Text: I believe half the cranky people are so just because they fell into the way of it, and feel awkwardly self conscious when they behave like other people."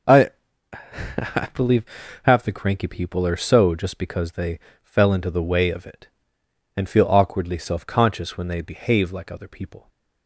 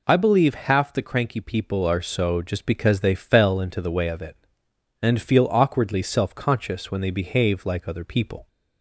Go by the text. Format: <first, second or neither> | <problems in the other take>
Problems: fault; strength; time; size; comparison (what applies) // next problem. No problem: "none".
second | says "I" twice; at 0.7 s // pauses between "believe" and "half"; at 1.8 s; 0.38 s long // pauses between "they" and "fell"; slight; at 4.5 s; 0.24 s long